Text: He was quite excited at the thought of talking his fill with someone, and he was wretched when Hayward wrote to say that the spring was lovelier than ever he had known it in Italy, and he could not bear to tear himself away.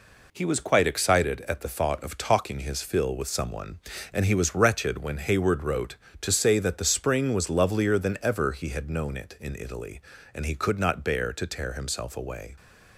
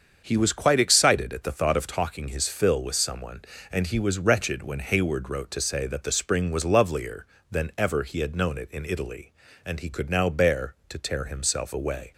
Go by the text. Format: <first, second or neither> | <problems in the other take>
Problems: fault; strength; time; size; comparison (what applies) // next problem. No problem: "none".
first | starts louder than the rest; until 1.2 s; 7 dB // says "now" for "not"; at 10.0 s